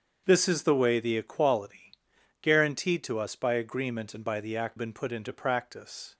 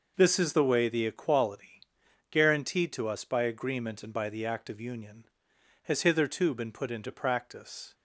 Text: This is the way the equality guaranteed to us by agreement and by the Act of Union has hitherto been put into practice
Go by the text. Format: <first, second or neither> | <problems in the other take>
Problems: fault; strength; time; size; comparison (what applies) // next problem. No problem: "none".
second | starts louder than the rest; until 1.2 s; 7 dB // pauses between "equality" and "guaranteed"; noticeable; at 1.9 s; 0.48 s long; noticeable in the second // skips "of Union has hitherto"; at 4.7 s